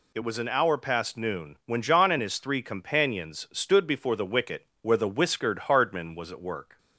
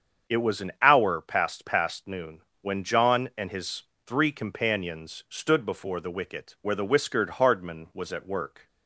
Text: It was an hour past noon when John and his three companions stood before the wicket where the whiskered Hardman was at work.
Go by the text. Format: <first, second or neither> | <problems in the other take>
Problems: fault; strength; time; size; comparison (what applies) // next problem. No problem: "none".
first | starts louder than the rest; strong; until 1.4 s; 7.5 dB // says "past" twice; at 1.6 s // pauses between "noon" and "when"; slight; at 2.4 s; 0.20 s long // pauses between "his" and "three"; slight; at 3.8 s; 0.22 s long